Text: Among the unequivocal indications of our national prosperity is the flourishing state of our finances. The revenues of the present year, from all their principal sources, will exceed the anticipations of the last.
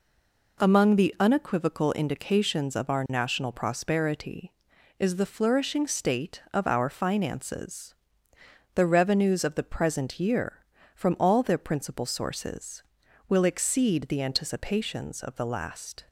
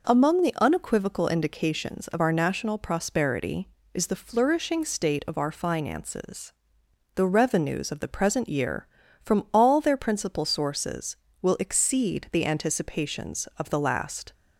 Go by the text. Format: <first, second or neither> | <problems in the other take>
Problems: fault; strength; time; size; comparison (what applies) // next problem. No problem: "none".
second | stays silent before the first word; slight; until 0.5 s; 0.5 s long